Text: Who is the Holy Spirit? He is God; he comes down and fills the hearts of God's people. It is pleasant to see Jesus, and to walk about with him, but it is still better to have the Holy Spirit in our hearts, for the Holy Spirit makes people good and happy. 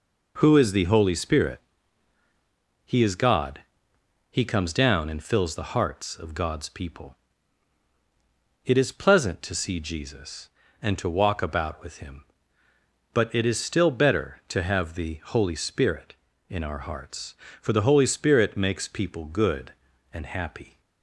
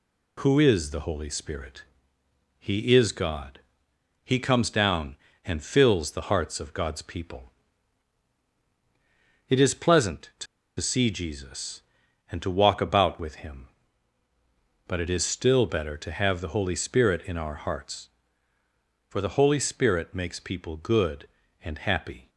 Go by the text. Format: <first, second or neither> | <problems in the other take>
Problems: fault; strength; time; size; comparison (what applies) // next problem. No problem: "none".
first | pauses between "to" and "see"; slight; at 10.4 s; 0.33 s long